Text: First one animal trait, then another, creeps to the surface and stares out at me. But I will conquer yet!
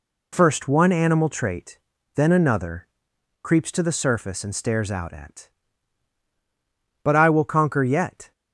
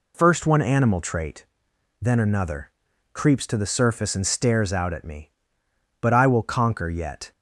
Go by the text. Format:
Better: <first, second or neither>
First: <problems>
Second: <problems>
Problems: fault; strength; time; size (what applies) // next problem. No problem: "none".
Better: second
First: skips "me"; at 6.2 s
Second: none